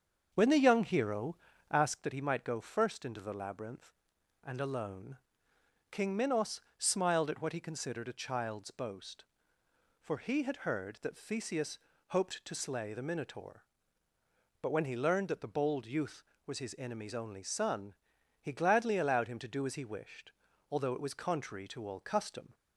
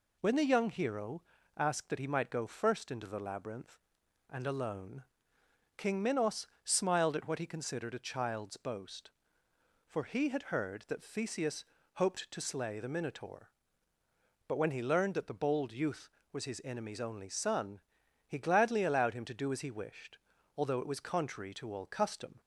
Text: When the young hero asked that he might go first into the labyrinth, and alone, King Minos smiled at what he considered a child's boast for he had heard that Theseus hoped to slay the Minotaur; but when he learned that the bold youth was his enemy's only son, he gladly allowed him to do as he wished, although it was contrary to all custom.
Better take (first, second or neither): second